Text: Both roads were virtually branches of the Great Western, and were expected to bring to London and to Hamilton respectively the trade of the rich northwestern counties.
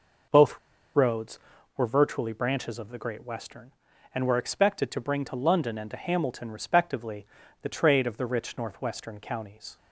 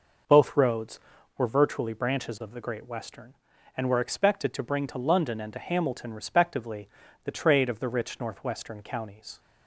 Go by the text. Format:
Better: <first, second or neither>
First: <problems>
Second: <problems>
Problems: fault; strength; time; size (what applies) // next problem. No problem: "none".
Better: second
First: pauses between "Both" and "roads"; at 0.5 s; 0.37 s long // pauses between "respectively" and "the"; slight; at 7.2 s; 0.36 s long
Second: pauses between "respectively" and "the"; slight; at 6.8 s; 0.36 s long